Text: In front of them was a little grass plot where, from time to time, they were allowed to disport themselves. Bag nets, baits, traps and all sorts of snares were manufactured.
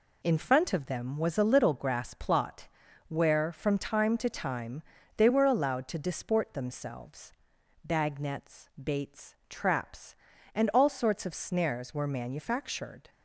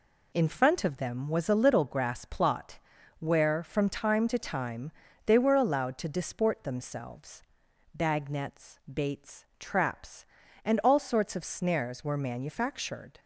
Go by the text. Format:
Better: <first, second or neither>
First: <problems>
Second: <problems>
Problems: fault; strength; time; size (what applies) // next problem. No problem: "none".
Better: neither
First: pauses between "plot" and "where"; at 2.6 s; 0.40 s long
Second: pauses between "plot" and "where"; at 2.7 s; 0.40 s long